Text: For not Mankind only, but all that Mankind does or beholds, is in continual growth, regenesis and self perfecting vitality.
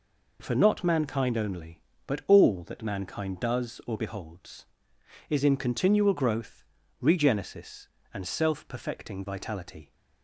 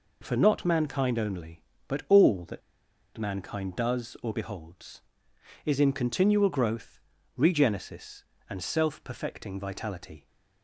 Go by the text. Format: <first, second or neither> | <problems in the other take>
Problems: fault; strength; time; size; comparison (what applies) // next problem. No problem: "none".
first | pauses between "that" and "Mankind"; noticeable; at 2.6 s; 0.56 s long